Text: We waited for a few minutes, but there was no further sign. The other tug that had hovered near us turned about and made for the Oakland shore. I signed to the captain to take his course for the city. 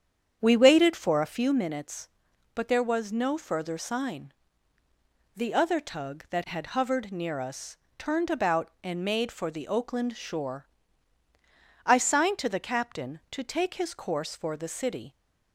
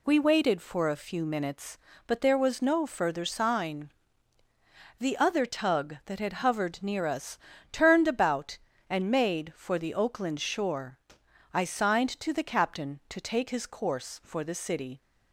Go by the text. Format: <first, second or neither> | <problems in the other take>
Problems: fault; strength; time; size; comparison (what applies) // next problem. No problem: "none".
second | starts louder than the rest; strong; until 1.5 s; 8 dB // pauses between "us" and "turned"; slight; at 7.7 s; 0.22 s long; slight in the second